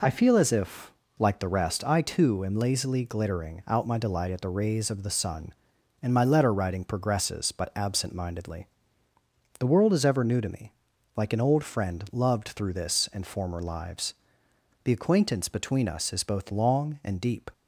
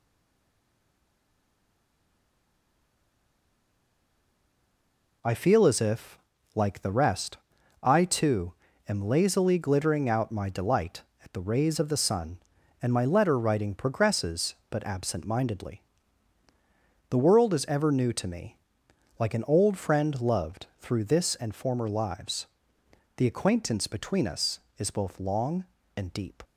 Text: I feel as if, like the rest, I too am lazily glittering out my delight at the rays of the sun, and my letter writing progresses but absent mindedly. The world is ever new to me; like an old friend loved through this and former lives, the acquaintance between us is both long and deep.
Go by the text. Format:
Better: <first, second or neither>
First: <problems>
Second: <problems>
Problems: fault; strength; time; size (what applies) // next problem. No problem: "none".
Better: first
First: none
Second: stays silent before the first word; strong; until 5.2 s; 5.2 s long // pauses between "too" and "am"; slight; at 8.5 s; 0.34 s long